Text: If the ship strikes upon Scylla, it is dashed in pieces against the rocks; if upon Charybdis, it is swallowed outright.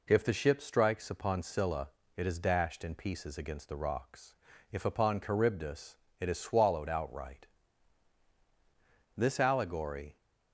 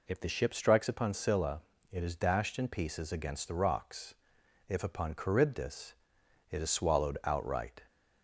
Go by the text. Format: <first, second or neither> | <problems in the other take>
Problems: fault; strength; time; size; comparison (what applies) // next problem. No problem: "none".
second | goes on to say "This allegory"; noticeable; from 9.1 s on; 0.98 s long